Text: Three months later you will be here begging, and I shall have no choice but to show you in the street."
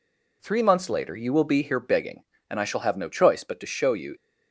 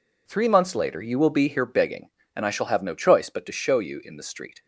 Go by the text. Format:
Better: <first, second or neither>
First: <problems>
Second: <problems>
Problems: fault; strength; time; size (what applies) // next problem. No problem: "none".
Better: second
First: stops before "in the street"; at 4.1 s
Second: none